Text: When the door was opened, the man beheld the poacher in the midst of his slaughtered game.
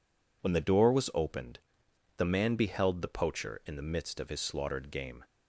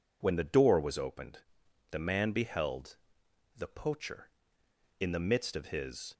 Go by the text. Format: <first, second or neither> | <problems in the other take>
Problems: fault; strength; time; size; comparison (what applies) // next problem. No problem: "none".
first | pauses between "beheld" and "the"; noticeable; at 2.9 s; 0.60 s long // stops before "slaughtered game"; at 6.1 s